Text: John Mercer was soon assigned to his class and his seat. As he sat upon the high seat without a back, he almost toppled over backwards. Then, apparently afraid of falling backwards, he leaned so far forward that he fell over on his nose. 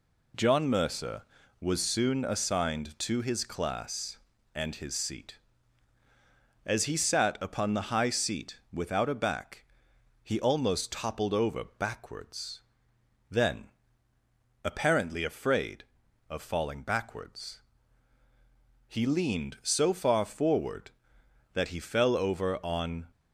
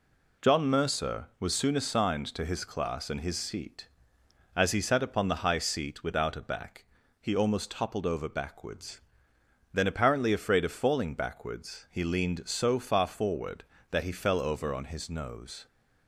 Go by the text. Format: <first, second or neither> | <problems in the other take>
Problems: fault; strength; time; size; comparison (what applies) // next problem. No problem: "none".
second | pauses between "seat" and "without"; slight; at 8.5 s; 0.16 s long // stops before "his nose"; at 23.1 s